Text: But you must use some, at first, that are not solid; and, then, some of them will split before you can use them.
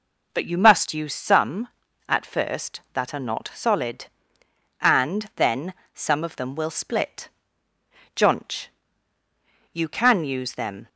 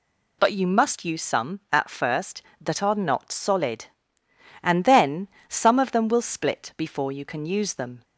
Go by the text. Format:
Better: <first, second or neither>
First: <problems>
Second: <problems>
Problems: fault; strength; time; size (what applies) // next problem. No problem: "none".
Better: second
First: says "jonch" for "before"; at 8.1 s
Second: none